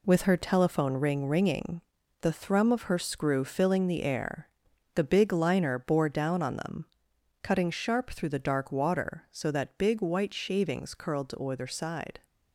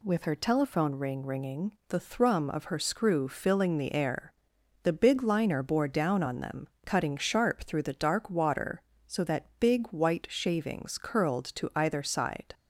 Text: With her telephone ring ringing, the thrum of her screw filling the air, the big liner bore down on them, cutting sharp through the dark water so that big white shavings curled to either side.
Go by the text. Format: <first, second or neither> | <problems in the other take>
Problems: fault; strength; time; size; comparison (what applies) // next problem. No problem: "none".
second | gets quieter; throughout; 7 dB